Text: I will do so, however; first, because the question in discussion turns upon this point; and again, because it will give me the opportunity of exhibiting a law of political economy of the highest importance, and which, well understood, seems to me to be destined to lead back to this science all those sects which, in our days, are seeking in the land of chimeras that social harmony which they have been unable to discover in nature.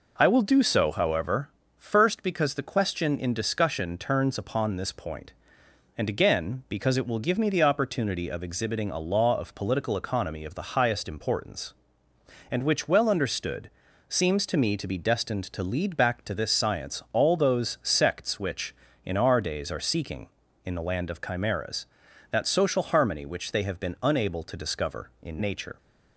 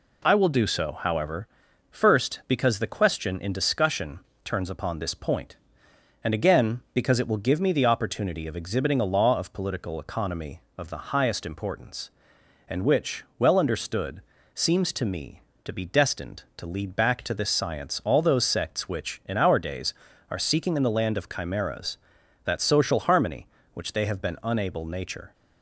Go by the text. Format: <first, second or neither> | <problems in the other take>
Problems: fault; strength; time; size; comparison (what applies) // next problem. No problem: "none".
first | pauses between "discussion" and "turns"; slight; at 4.1 s; 0.26 s long // skips "to discover in"; at 24.8 s